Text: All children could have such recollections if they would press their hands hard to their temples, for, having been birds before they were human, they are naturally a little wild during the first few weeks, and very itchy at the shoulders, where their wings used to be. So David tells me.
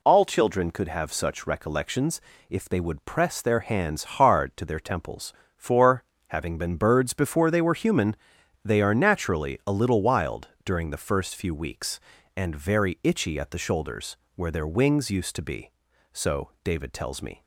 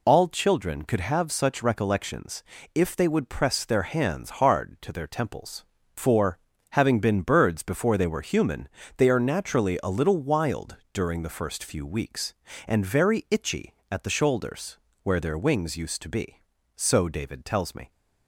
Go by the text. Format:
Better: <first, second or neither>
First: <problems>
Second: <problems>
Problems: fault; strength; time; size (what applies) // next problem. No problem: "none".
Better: neither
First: pauses between "recollections" and "if"; slight; at 2.1 s; 0.30 s long // pauses between "wild" and "during"; slight; at 10.4 s; 0.16 s long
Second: pauses between "recollections" and "if"; slight; at 2.4 s; 0.32 s long // pauses between "wild" and "during"; slight; at 10.7 s; 0.16 s long